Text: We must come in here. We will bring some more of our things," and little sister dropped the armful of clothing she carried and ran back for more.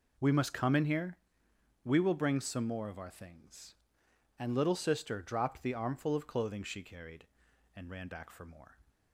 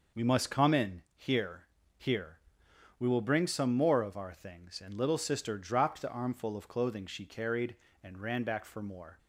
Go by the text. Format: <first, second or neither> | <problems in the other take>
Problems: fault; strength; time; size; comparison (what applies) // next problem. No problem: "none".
first | says "here" twice; at 1.9 s